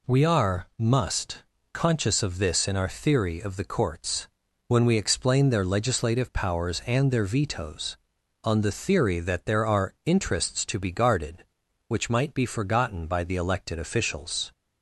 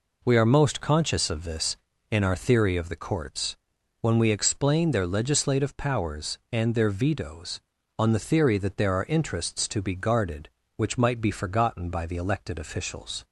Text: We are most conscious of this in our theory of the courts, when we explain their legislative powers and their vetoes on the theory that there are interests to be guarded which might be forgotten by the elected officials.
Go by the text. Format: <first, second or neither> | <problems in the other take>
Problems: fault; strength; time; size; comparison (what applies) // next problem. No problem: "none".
second | says "must" for "most"; at 0.7 s